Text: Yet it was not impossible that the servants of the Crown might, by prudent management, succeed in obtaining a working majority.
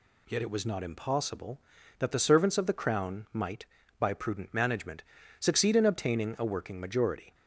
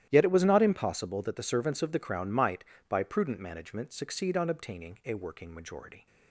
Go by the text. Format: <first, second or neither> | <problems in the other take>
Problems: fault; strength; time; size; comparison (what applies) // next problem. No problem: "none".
first | starts louder than the rest; strong; until 1.1 s; 12 dB // says "on" for "in"; at 4.3 s